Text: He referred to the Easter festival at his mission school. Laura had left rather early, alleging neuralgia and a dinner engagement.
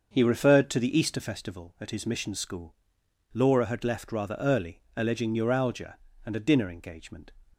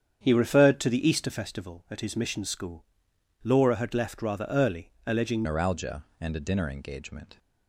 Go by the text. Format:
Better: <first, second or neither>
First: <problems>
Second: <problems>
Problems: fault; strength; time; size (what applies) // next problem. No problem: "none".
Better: first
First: starts louder than the rest; until 1.1 s; 6.5 dB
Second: starts louder than the rest; strong; until 1.2 s; 8 dB // changes voice at "neuralgia"; from 5.4 s on; 1.9 s long